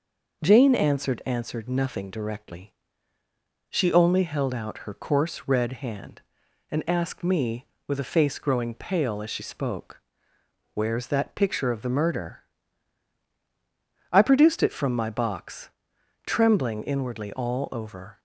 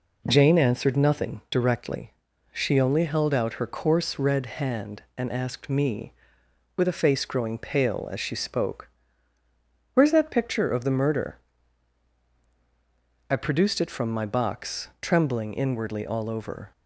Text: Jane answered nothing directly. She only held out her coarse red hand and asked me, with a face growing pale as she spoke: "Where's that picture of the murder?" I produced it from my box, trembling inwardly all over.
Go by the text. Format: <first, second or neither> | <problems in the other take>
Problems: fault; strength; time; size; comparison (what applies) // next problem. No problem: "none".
second | says "answered" twice; at 1.2 s